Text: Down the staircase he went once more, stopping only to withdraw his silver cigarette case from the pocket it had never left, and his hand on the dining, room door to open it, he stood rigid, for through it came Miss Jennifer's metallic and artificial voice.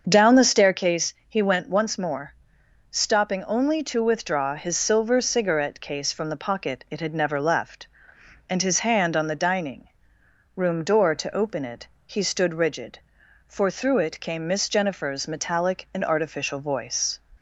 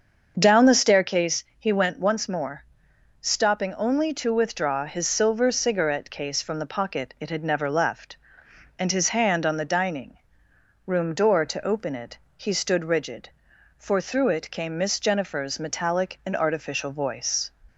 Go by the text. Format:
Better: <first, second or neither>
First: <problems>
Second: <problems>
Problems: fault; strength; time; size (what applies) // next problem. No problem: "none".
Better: neither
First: starts louder than the rest; until 1.0 s; 6.5 dB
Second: starts louder than the rest; until 1.3 s; 6.5 dB